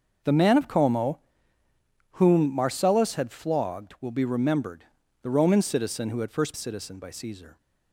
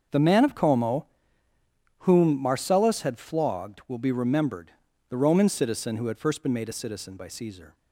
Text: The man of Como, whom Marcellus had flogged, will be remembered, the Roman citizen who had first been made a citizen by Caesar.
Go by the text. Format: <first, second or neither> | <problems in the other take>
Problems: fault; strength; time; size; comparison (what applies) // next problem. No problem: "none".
second | starts louder than the rest; noticeable; until 2.1 s; 6 dB; also in the second // skips "been made a"; at 6.5 s